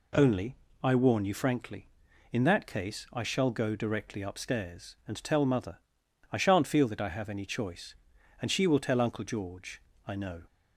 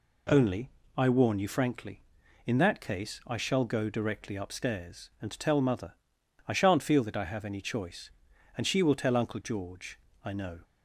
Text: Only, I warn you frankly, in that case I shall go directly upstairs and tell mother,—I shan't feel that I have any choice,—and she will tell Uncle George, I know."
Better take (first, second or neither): neither